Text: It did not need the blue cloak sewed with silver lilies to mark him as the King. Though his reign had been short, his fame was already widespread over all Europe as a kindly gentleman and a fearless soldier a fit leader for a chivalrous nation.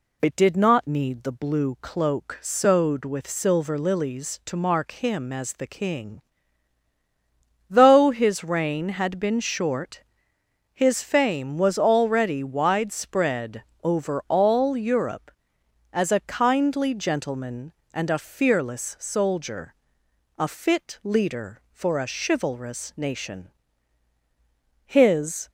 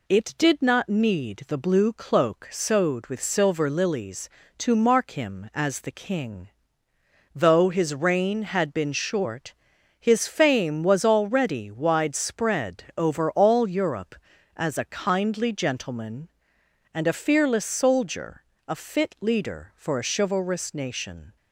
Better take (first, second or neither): second